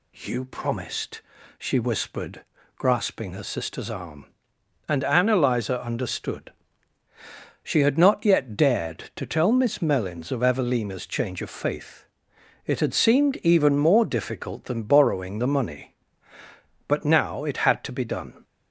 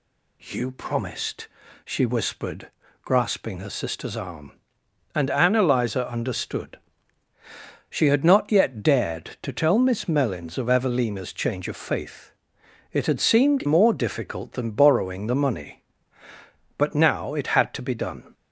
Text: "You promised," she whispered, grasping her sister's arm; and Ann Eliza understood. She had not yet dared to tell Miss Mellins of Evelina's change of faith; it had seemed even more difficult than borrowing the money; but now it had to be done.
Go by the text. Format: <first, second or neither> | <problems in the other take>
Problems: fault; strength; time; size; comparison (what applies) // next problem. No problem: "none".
first | skips "even"; at 13.6 s